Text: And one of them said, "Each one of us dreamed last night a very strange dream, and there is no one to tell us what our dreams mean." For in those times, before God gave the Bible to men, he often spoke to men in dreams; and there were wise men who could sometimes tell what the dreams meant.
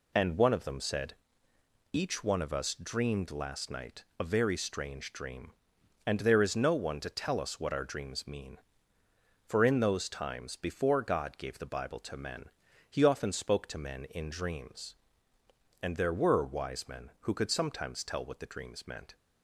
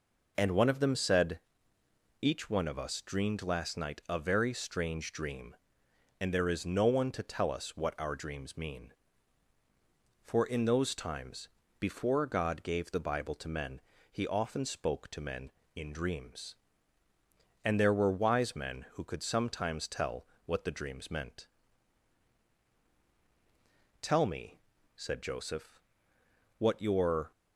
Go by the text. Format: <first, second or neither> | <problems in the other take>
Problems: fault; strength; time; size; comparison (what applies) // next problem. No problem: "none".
first | pauses between "tell" and "what"; slight; at 20.2 s; 0.18 s long // goes on to say "Tell me said Joseph what your"; strong; from 24.0 s on; 3.3 s long